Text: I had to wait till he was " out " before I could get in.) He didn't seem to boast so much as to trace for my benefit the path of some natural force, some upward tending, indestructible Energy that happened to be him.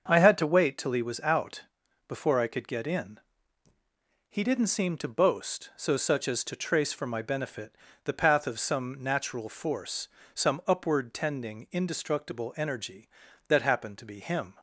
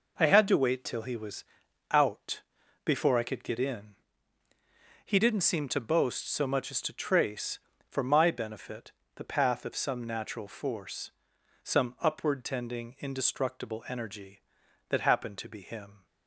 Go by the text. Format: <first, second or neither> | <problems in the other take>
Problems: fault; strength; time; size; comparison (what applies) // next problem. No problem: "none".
second | starts louder than the rest; until 1.0 s; 6.5 dB // says "such" for "much"; at 5.9 s // pauses between "benefit" and "the"; slight; at 7.7 s; 0.30 s long; slight in the second